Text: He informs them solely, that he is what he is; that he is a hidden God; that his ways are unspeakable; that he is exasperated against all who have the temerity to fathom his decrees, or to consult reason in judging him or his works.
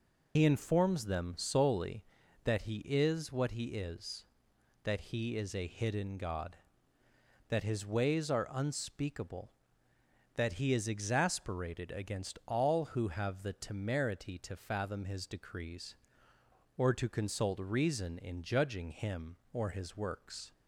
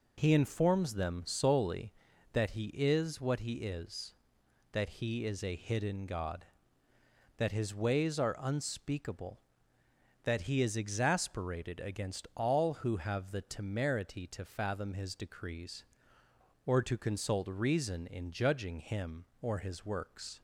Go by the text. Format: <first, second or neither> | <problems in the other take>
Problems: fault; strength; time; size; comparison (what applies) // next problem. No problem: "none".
second | loses the start of "He"; at 0.3 s; 60 ms